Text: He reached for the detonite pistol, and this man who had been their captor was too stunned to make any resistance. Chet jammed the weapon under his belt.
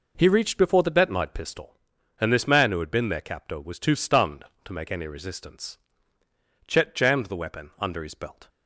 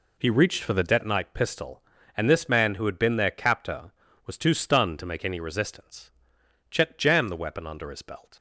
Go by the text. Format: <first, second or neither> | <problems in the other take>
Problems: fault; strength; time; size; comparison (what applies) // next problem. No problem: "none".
second | says "before" for "for"; at 0.5 s